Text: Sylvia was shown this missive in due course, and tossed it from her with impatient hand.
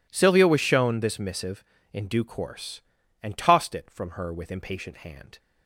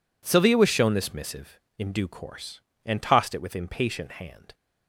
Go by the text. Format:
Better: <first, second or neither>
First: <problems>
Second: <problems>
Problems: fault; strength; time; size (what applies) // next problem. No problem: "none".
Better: first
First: none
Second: skips "from her"; at 3.4 s